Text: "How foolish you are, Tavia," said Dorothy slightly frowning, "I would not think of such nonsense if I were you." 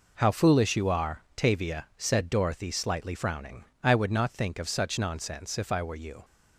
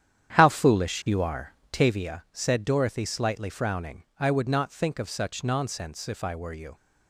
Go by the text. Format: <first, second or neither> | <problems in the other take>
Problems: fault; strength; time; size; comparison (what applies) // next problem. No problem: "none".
first | starts louder than the rest; strong; until 1.9 s; 9.5 dB